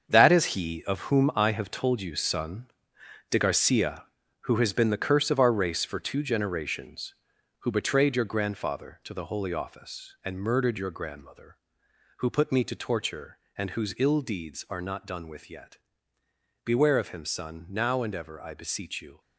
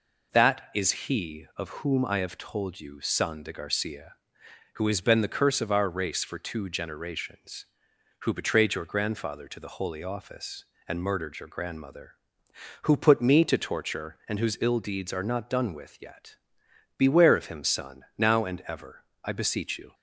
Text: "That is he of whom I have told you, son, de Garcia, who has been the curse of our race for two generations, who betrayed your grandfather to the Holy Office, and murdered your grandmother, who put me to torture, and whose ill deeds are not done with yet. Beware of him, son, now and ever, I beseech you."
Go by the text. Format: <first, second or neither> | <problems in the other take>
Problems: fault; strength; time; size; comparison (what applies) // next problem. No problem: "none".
second | gets quieter; strong; throughout; 10 dB